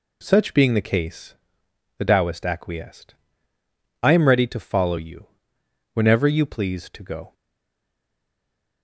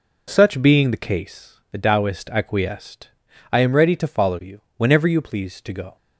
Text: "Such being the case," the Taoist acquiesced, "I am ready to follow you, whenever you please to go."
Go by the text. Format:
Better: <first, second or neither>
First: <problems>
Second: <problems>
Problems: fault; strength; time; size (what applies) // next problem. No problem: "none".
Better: second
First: stays silent after the last word; noticeable; from 7.3 s on; 1.5 s long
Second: none